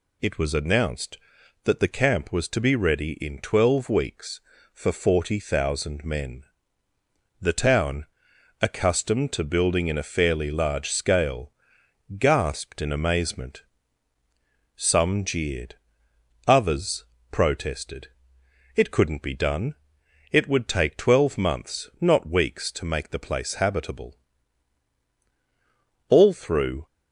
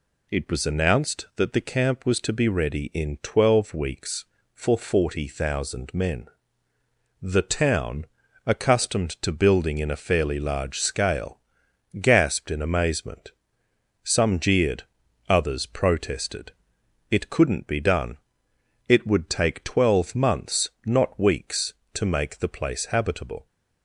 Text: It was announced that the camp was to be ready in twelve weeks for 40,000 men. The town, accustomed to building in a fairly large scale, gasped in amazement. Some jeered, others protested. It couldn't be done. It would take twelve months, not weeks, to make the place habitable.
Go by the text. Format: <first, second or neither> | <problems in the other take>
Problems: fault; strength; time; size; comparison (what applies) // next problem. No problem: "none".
second | pauses between "others" and "protested"; slight; at 17.0 s; 0.28 s long // goes on to say "All through"; noticeable; from 26.0 s on; 0.76 s long